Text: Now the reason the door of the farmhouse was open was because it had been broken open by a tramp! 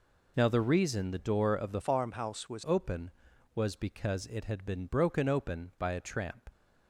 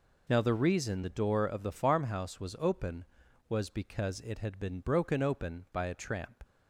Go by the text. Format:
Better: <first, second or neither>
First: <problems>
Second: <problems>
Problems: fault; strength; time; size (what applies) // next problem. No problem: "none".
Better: second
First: changes voice from "farmhouse" to "was"; from 1.8 to 2.6 s; 0.8 s long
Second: none